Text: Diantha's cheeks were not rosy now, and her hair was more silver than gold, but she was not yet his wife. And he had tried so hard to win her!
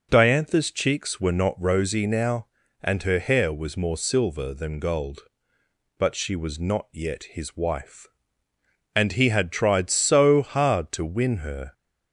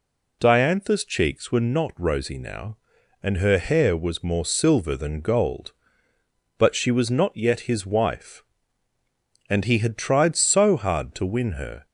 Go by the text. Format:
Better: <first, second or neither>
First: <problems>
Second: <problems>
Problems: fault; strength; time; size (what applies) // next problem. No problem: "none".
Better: neither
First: none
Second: none